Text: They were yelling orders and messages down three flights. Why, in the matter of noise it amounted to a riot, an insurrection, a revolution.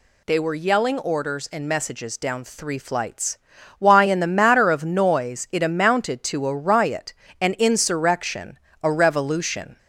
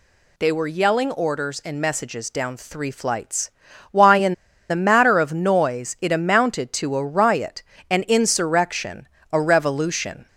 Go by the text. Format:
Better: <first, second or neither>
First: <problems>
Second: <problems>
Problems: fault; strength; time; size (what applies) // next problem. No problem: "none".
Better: first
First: none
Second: pauses between "in" and "the"; slight; at 4.3 s; 0.35 s long